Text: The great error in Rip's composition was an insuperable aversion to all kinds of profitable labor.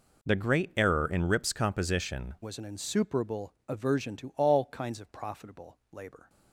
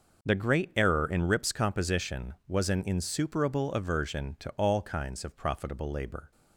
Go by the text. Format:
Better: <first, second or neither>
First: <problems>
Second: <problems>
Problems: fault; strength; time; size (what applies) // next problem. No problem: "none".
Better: second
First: changes voice at "was"; from 2.4 s on; 3.8 s long // pauses between "insuperable" and "aversion"; slight; at 3.5 s; 0.16 s long // pauses between "profitable" and "labor"; slight; at 5.7 s; 0.16 s long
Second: none